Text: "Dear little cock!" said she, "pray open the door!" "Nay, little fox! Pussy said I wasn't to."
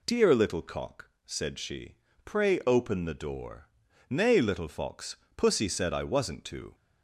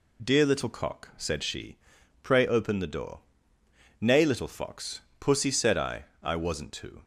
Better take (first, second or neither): first